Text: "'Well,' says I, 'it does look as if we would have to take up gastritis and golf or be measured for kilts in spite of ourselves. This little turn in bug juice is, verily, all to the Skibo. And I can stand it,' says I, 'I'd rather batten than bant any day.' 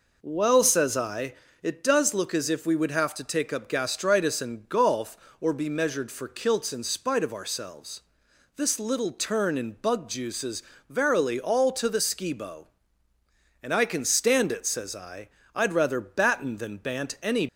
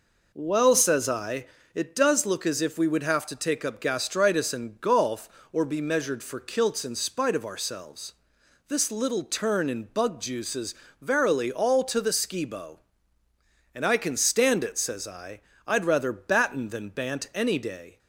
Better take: second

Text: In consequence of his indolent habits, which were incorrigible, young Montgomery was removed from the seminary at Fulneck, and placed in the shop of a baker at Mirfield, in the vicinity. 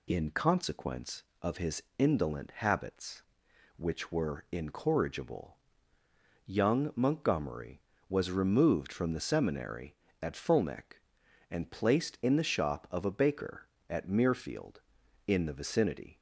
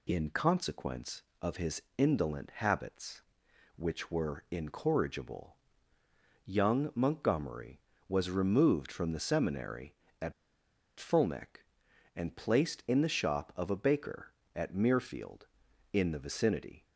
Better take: first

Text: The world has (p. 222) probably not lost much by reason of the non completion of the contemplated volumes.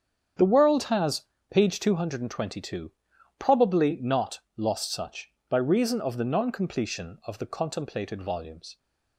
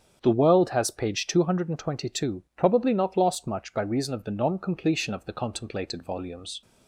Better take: second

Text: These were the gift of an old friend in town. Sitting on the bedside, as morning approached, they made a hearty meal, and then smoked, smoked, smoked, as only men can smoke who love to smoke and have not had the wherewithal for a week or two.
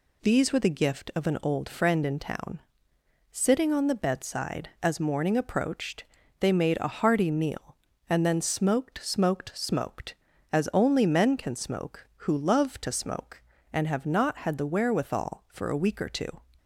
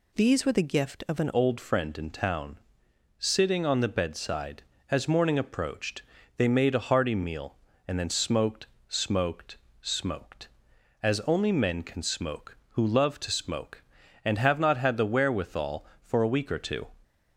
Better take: first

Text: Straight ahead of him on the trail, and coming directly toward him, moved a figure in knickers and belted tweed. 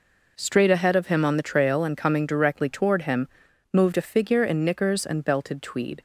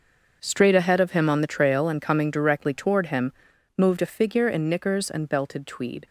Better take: first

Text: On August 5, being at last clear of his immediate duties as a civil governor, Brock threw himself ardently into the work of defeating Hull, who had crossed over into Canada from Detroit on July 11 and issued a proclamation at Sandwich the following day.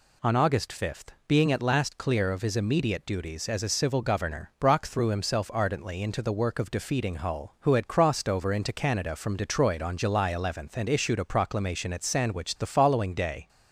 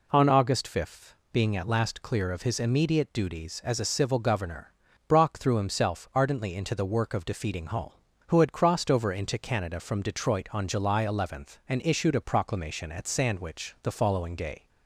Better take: neither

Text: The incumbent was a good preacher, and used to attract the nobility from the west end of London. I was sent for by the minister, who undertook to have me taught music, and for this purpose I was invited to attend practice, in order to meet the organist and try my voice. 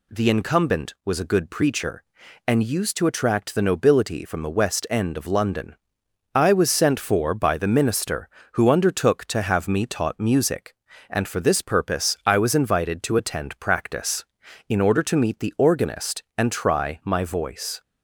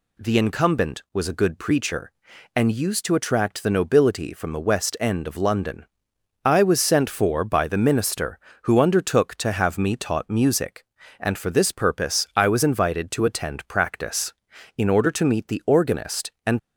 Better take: first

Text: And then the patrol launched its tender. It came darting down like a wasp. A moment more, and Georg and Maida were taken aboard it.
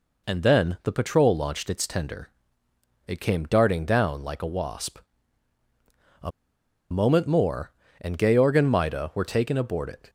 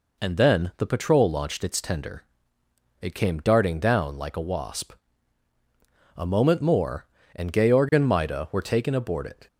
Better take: second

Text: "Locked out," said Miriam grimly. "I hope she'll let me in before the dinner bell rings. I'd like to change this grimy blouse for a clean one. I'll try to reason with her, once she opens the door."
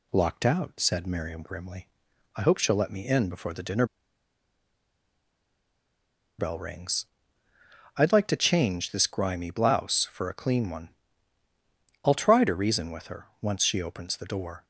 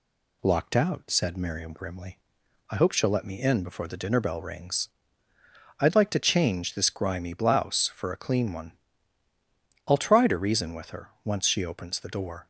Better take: second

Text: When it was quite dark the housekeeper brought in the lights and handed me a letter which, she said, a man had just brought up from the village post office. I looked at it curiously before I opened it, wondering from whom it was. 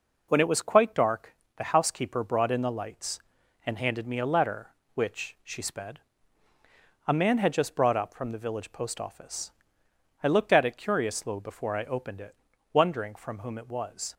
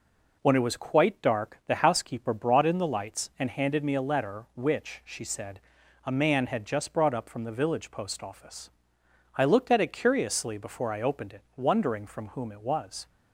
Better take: second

